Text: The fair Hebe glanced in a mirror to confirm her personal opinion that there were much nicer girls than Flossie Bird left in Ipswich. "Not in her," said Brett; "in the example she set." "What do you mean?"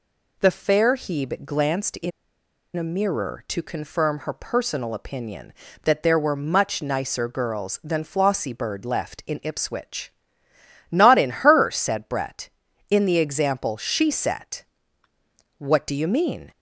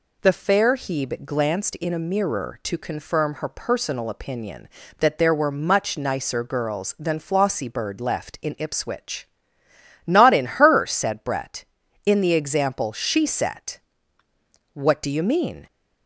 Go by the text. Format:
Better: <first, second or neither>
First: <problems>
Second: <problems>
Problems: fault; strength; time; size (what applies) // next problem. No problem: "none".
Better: second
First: pauses between "in" and "a"; noticeable; at 2.1 s; 0.66 s long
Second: none